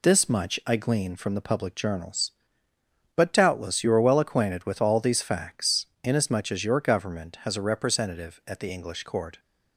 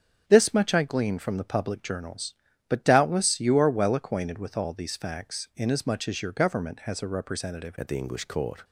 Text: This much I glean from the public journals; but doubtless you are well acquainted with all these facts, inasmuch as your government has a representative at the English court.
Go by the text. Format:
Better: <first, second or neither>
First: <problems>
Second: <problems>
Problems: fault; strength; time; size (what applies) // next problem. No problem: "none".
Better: first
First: none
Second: starts louder than the rest; strong; until 1.2 s; 7.5 dB // changes voice at "at"; from 7.7 s on; 0.9 s long